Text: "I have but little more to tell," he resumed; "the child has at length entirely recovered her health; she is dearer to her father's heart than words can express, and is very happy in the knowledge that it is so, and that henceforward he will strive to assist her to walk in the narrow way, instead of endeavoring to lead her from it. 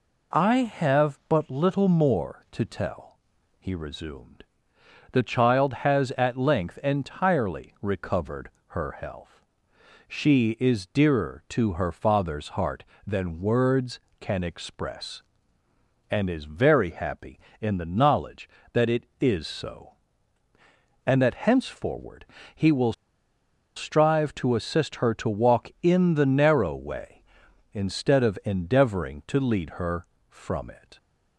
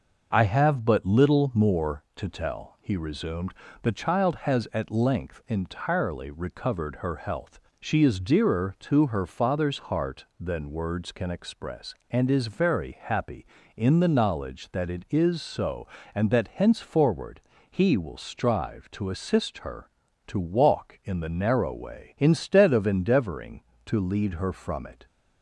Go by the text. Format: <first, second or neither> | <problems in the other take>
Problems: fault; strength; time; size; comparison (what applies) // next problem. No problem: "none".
second | pauses between "recovered" and "her"; slight; at 8.4 s; 0.18 s long // pauses between "henceforward" and "he"; slight; at 22.2 s; 0.32 s long; slight in the second // pauses between "will" and "strive"; noticeable; at 22.9 s; 0.82 s long